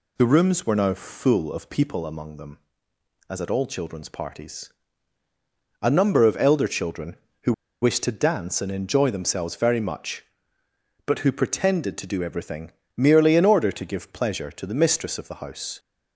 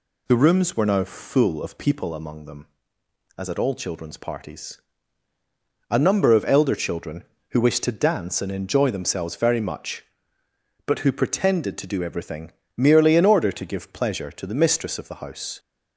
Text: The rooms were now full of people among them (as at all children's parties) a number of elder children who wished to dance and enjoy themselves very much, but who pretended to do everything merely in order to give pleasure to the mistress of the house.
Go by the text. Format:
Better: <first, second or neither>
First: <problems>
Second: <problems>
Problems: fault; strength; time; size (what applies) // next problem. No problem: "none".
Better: second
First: pauses between "who" and "wished"; slight; at 7.5 s; 0.30 s long // pauses between "everything" and "merely"; slight; at 12.7 s; 0.24 s long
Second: pauses between "everything" and "merely"; slight; at 12.5 s; 0.24 s long